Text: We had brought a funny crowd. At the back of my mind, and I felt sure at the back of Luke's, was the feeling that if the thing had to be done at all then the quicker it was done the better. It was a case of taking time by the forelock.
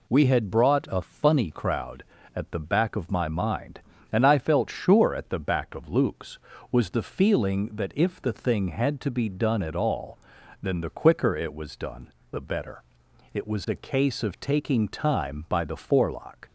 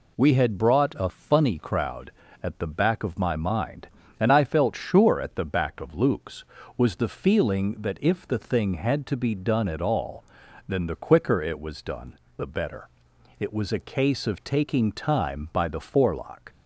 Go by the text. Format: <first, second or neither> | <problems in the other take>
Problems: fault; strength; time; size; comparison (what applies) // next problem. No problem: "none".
neither | pauses between "all" and "then"; the same in both // pauses between "done" and "the"; slight; the same in both